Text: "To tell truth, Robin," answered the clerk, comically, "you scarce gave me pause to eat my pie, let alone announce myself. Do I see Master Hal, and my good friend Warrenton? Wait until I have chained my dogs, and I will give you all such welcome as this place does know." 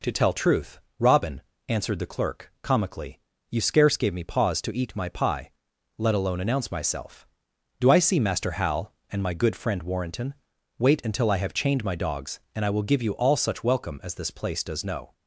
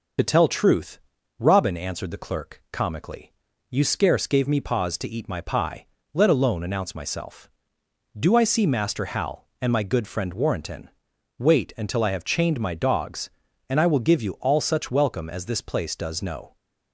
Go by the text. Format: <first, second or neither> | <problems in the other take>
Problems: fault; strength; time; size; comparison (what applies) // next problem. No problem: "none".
first | loses the start of "To"; at 0.1 s; 30 ms